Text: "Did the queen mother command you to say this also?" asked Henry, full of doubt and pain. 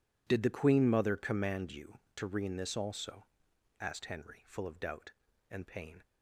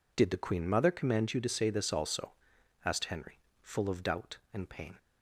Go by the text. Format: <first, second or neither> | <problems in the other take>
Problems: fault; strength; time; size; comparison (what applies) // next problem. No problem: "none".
second | says "rean" for "say"; at 2.2 s